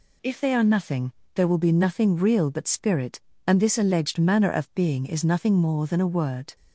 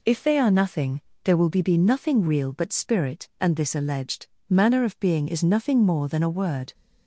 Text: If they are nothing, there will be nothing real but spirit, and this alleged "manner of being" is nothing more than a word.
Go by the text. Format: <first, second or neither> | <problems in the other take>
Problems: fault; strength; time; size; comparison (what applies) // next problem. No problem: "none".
first | says "be" twice; at 1.6 s // pauses between "alleged" and "manner"; slight; at 4.2 s; 0.24 s long